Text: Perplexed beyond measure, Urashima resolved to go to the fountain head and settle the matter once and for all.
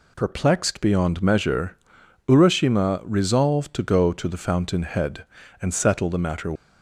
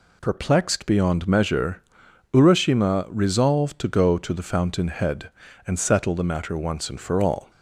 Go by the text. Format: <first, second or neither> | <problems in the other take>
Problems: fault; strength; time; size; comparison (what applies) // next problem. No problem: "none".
second | stops before "once and for all"; at 6.5 s